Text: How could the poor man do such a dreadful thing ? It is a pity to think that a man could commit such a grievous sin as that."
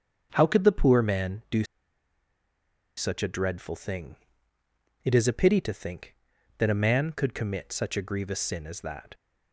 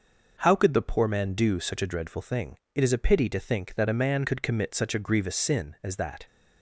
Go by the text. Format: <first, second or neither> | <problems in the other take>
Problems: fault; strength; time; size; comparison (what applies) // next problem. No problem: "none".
second | starts louder than the rest; strong; until 1.3 s; 7.5 dB // pauses between "do" and "such"; strong; at 1.6 s; 1.3 s long